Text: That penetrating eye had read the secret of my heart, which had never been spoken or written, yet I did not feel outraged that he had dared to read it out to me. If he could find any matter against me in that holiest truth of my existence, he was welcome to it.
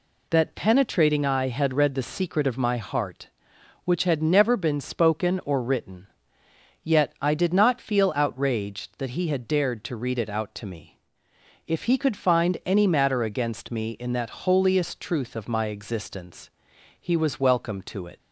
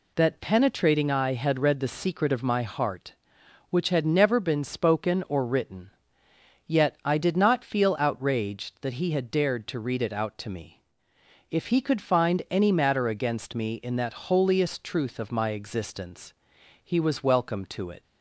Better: neither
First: none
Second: none

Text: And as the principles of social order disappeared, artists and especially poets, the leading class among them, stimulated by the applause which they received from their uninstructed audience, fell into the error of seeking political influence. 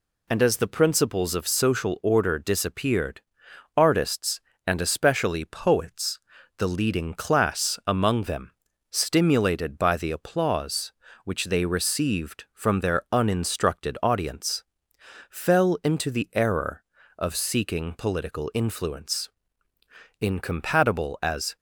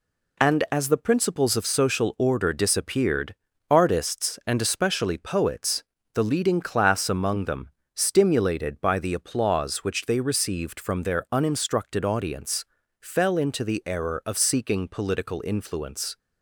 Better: second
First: goes on to say "Incompatible as"; from 20.1 s on; 1.3 s long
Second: none

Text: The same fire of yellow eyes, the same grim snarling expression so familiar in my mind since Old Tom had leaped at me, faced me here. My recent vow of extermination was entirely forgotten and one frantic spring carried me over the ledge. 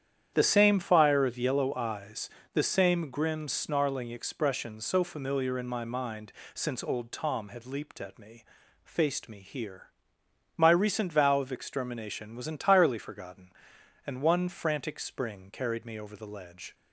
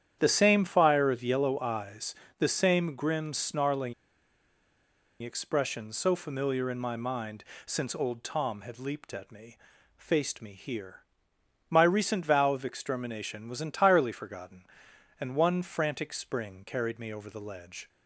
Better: first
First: starts louder than the rest; strong; until 1.3 s; 9.5 dB // pauses between "mind" and "since"; slight; at 6.3 s; 0.22 s long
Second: starts louder than the rest; strong; until 1.2 s; 9.5 dB // pauses between "snarling" and "expression"; strong; at 3.9 s; 1.2 s long // pauses between "mind" and "since"; slight; at 7.4 s; 0.22 s long

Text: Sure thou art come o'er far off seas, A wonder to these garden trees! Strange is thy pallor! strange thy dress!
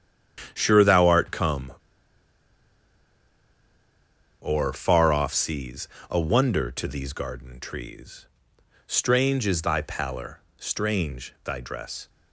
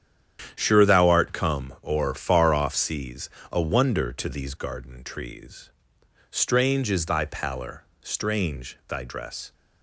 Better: second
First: starts louder than the rest; strong; until 1.5 s; 10 dB // pauses between "come" and "o'er"; strong; at 1.7 s; 2.6 s long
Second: starts louder than the rest; strong; until 1.5 s; 9.5 dB

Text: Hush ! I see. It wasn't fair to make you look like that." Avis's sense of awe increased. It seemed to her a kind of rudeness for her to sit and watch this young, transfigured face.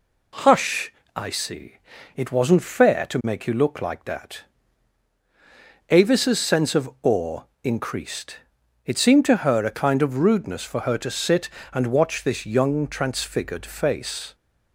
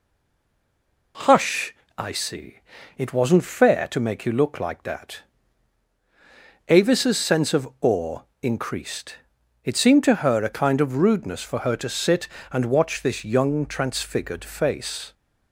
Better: first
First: pauses between "awe" and "increased"; slight; at 7.4 s; 0.18 s long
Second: stays silent before the first word; until 1.1 s; 1.1 s long // pauses between "awe" and "increased"; slight; at 8.2 s; 0.18 s long

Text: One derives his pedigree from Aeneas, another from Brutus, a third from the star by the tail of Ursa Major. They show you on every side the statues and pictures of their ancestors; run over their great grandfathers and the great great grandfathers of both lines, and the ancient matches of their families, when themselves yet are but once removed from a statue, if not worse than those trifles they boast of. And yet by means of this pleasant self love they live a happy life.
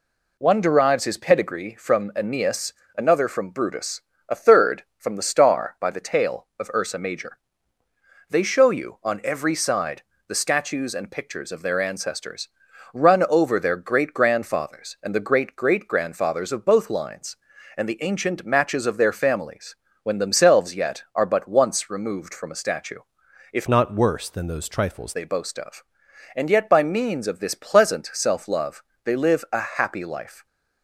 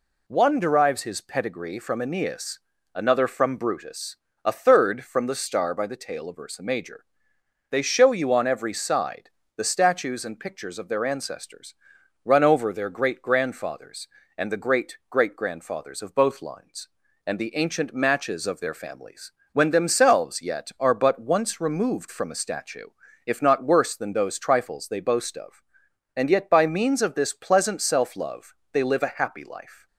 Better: second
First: pauses between "side" and "the"; slight; at 10.0 s; 0.24 s long // changes voice from "not" to "trifles"; from 23.6 to 25.1 s; 1.5 s long // pauses between "love" and "they"; slight; at 28.8 s; 0.22 s long // pauses between "a" and "happy"; slight; at 29.5 s; 0.18 s long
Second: pauses between "side" and "the"; slight; at 9.2 s; 0.26 s long // pauses between "love" and "they"; slight; at 28.5 s; 0.20 s long

